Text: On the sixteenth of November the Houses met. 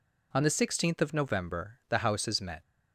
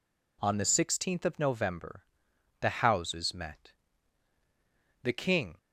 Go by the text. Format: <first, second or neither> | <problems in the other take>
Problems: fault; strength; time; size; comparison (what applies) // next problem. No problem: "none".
first | pauses between "November" and "the"; noticeable; at 2.0 s; 0.56 s long // goes on to say "The King"; from 5.0 s on; 0.56 s long